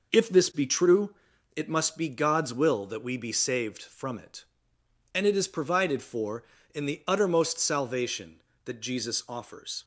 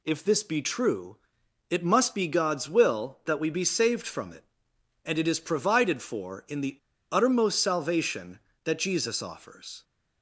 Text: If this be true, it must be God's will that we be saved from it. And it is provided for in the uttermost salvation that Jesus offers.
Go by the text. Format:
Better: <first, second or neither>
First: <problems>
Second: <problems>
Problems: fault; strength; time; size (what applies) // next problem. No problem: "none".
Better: first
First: none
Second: pauses between "the" and "uttermost"; slight; at 6.7 s; 0.35 s long